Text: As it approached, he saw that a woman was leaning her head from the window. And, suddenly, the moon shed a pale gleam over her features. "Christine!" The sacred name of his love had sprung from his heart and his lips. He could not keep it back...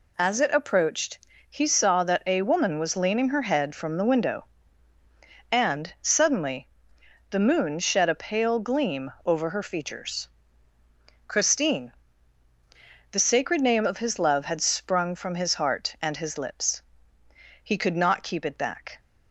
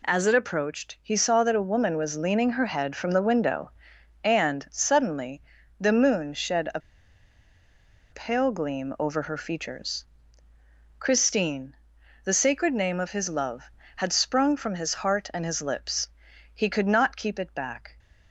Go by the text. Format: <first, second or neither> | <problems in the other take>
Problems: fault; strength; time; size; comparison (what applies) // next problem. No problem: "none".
first | pauses between "a" and "pale"; strong; at 6.7 s; 1.3 s long